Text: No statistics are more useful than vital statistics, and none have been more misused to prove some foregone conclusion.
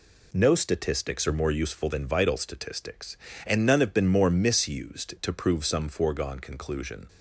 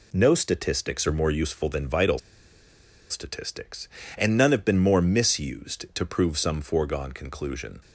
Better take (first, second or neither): first